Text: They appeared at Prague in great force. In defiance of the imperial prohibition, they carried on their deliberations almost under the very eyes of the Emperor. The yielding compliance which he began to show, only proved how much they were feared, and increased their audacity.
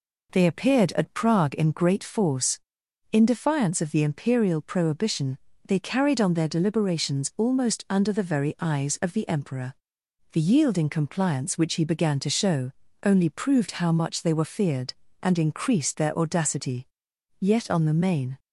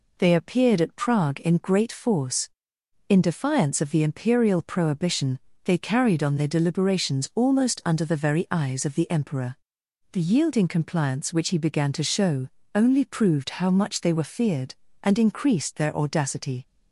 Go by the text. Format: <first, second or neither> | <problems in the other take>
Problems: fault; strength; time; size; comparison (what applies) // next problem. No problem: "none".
second | goes on to say "Yet on the main"; noticeable; from 17.4 s on; 0.98 s long